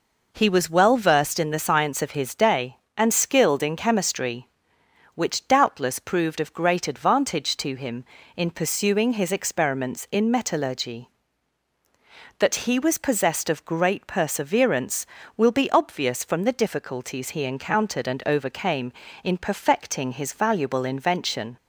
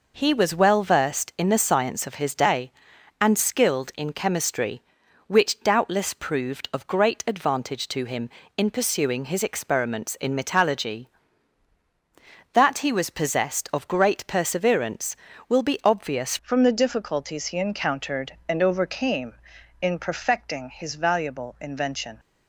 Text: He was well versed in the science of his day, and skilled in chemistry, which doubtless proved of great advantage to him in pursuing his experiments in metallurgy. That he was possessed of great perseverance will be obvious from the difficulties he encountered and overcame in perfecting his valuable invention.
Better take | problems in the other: first | changes voice at "from"; from 16.4 s on; 5.7 s long

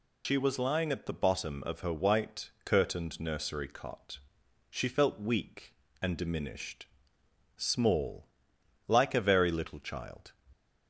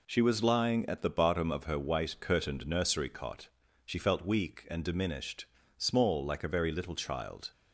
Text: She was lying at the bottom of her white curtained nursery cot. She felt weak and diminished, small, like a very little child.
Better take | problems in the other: second | loses the start of "She"; at 0.2 s; 90 ms

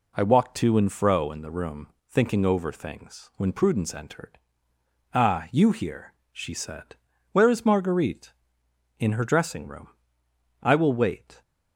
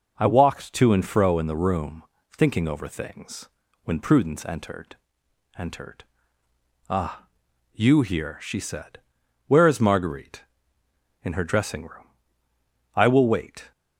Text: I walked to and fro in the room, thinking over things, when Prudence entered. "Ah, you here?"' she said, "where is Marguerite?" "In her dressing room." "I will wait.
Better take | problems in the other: first | says "entered" twice; at 5.5 s

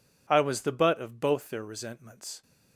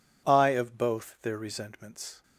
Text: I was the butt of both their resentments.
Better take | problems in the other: first | skips "was the butt"; at 0.5 s

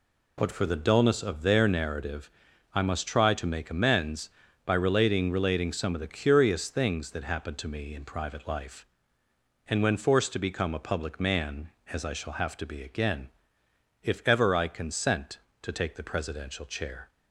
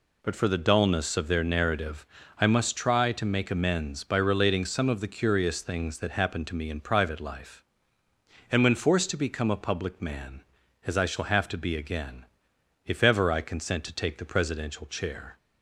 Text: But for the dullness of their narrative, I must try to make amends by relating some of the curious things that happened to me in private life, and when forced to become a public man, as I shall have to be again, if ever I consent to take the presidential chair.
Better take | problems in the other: second | says "relating" twice; at 5.3 s

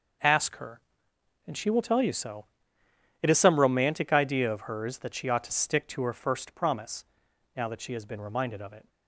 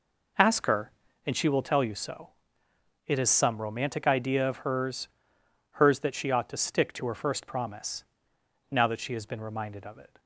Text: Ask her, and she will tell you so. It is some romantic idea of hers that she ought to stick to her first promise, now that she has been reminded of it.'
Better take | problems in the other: first | says "hers" twice; at 5.7 s

